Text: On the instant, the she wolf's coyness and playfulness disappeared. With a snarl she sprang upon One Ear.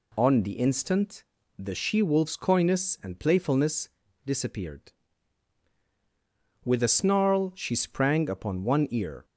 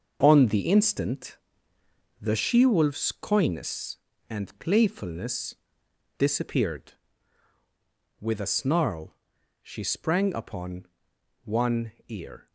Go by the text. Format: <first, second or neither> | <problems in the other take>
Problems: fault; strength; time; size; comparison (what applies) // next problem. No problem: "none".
first | gets quieter; strong; throughout; 9 dB // pauses between "playfulness" and "disappeared"; noticeable; at 5.5 s; 0.64 s long; also in the first // pauses between "snarl" and "she"; noticeable; at 9.1 s; 0.48 s long // pauses between "upon" and "One"; noticeable; at 10.8 s; 0.58 s long // pauses between "One" and "Ear"; slight; at 11.9 s; 0.16 s long